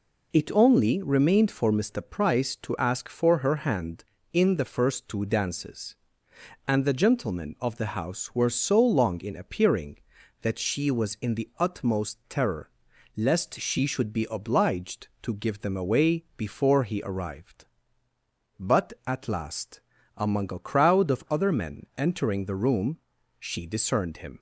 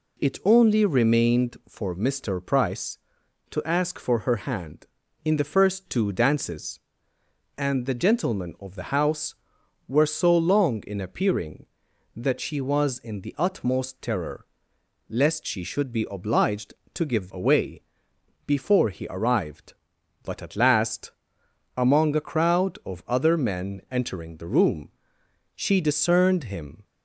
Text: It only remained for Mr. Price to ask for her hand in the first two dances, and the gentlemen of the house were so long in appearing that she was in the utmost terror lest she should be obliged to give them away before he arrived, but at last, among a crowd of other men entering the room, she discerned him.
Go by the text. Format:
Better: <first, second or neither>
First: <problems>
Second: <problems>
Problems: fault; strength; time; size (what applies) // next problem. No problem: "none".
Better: first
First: pauses between "terror" and "lest"; noticeable; at 12.6 s; 0.48 s long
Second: pauses between "terror" and "lest"; noticeable; at 14.4 s; 0.64 s long // skips "them"; at 17.3 s // pauses between "away" and "before"; noticeable; at 17.8 s; 0.64 s long